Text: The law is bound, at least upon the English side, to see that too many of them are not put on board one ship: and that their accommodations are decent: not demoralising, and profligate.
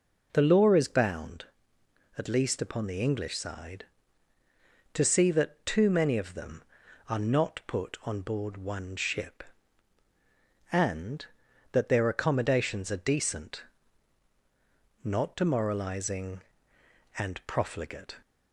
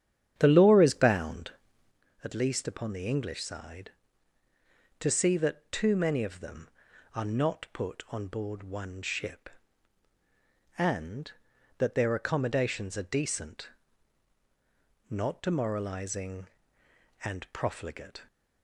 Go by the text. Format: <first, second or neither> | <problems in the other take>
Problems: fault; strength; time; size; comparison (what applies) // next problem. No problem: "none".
first | starts louder than the rest; strong; until 2.0 s; 9.5 dB